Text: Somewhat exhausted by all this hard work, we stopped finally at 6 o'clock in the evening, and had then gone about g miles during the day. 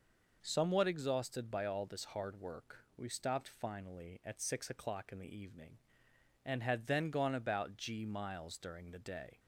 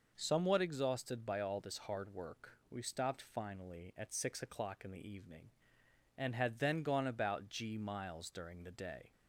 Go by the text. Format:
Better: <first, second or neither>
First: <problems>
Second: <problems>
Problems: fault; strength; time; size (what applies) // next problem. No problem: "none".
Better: neither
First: none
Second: none